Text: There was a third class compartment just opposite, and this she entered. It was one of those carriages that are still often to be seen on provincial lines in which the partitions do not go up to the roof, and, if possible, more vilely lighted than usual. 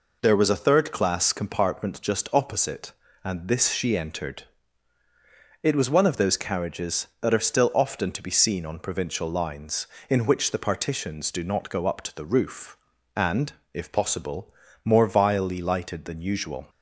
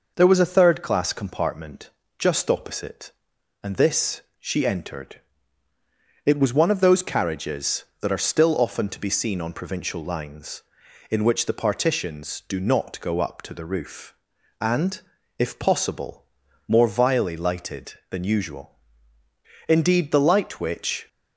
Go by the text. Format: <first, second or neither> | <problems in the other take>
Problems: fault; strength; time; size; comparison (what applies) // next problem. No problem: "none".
first | pauses between "compartment" and "just"; slight; at 1.8 s; 0.28 s long // pauses between "this" and "she"; slight; at 4.1 s; 0.18 s long // goes on to say "Indeed the light which"; from 19.6 s on; 1.4 s long